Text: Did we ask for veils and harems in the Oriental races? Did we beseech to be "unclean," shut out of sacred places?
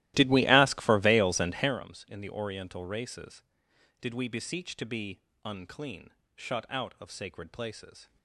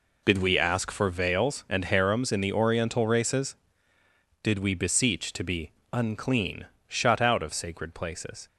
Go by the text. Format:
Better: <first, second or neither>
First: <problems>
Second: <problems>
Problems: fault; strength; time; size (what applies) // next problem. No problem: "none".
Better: second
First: starts louder than the rest; strong; until 1.8 s; 16 dB // pauses between "be" and "unclean"; slight; at 5.1 s; 0.24 s long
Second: pauses between "be" and "unclean"; slight; at 5.7 s; 0.20 s long